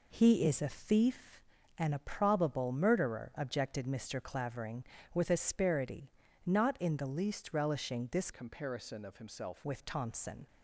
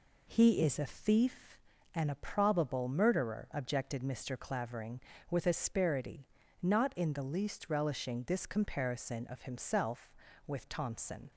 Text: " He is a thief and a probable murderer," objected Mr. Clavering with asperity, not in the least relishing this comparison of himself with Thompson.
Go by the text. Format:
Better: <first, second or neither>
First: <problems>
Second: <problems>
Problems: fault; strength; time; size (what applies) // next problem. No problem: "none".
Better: second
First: changes voice from "comparison" to "himself"; from 8.3 to 9.6 s; 1.3 s long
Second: none